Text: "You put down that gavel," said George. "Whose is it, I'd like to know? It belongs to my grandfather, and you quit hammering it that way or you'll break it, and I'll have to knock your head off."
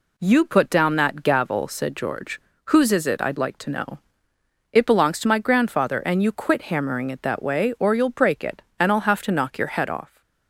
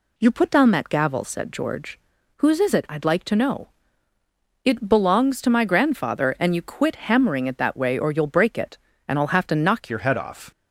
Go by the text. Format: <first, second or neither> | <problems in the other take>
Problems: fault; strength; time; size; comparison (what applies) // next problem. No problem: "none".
first | changes voice at "your"; from 9.8 s on; 0.7 s long